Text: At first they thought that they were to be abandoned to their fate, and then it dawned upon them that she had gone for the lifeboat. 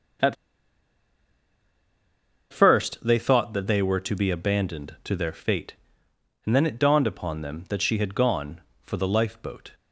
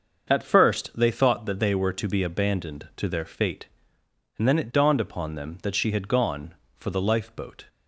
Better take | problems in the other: second | starts louder than the rest; until 3.4 s; 6.5 dB; also in the second // pauses between "At" and "first"; strong; at 0.3 s; 2.1 s long

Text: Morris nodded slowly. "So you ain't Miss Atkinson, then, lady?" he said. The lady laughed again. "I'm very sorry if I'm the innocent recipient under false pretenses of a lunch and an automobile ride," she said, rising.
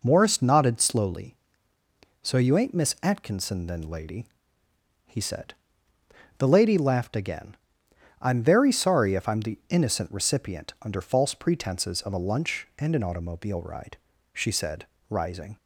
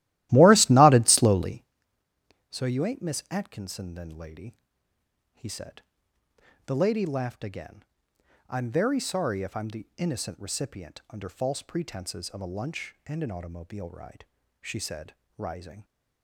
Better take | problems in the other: first | starts louder than the rest; strong; until 1.7 s; 15.5 dB

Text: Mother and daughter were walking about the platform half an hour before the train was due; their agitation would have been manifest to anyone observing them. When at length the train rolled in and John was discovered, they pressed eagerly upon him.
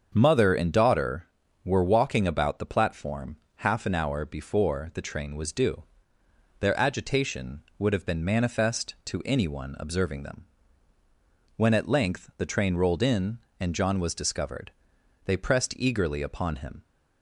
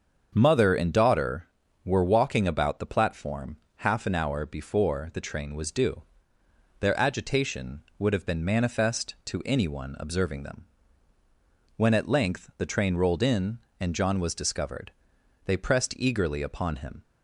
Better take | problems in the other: neither | starts louder than the rest; strong; the same in both // pauses between "platform" and "half"; slight; the same in both

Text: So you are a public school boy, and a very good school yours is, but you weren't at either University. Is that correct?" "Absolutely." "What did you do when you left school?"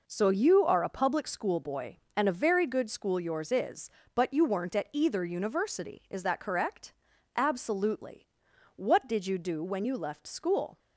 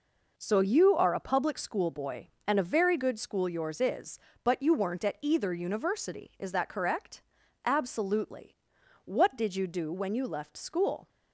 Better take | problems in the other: neither | none

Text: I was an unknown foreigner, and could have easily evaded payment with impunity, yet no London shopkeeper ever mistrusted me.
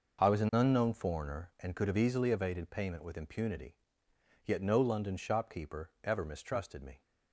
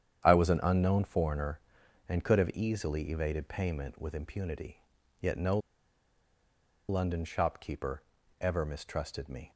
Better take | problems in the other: first | starts louder than the rest; strong; until 1.2 s; 9 dB // pauses between "no" and "London"; strong; at 5.5 s; 1.3 s long // pauses between "shopkeeper" and "ever"; slight; at 8.0 s; 0.36 s long

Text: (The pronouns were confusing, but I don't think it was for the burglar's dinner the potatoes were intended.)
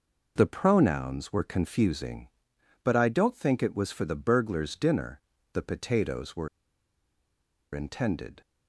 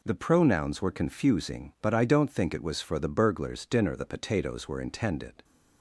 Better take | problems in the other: second | pauses between "dinner" and "the"; slight; at 5.2 s; 0.34 s long // pauses between "were" and "intended"; strong; at 6.4 s; 1.2 s long

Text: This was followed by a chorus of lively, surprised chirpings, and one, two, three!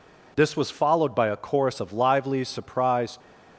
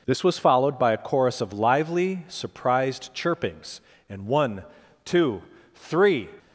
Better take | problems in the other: second | stops before "chirpings and one two three"; at 3.2 s

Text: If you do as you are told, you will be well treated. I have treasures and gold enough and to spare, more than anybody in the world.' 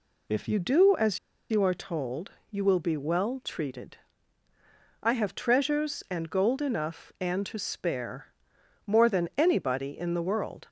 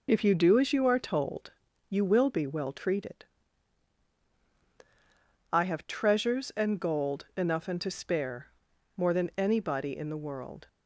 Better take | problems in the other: second | pauses between "as" and "you"; slight; at 1.1 s; 0.31 s long

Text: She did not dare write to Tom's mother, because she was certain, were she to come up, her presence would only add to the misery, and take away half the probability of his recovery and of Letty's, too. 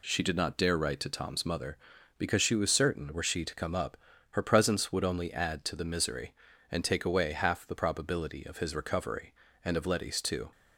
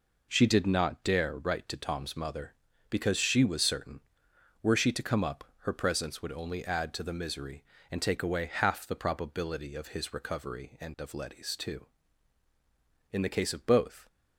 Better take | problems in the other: first | goes on to say "In the case of both"; noticeable; from 13.1 s on; 0.96 s long

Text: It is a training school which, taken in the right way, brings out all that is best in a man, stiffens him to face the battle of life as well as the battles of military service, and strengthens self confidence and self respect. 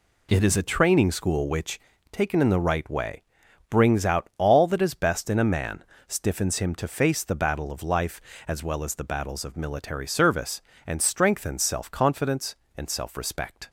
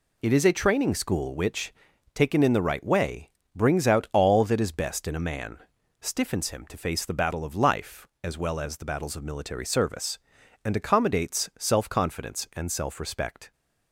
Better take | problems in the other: first | says "accommodates" for "strengthens"; at 10.7 s

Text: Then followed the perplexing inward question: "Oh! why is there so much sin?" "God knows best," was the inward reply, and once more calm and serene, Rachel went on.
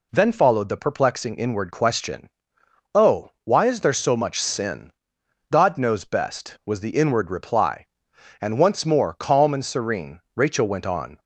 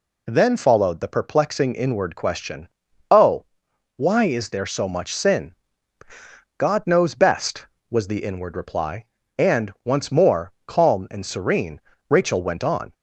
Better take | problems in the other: neither | none

